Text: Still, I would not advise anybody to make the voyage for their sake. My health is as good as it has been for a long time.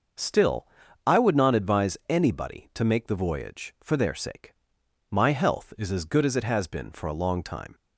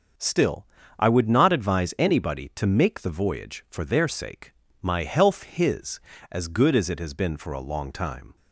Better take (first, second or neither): first